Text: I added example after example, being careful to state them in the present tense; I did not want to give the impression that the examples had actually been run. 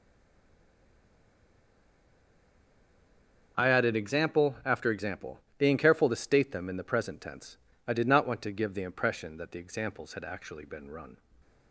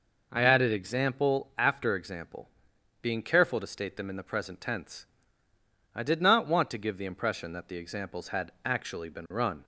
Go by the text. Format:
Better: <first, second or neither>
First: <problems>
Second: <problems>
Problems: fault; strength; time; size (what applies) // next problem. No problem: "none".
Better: second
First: stays silent before the first word; strong; until 3.5 s; 3.5 s long // starts louder than the rest; until 4.5 s; 6.5 dB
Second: none